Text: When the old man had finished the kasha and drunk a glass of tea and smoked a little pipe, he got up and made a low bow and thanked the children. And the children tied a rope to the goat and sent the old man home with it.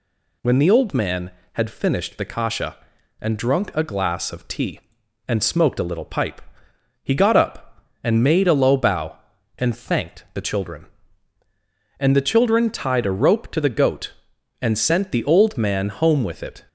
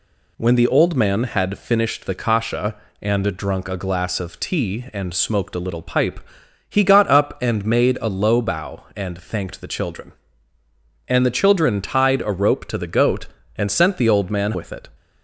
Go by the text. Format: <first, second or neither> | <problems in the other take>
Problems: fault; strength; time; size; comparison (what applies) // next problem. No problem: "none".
first | skips "home"; at 14.5 s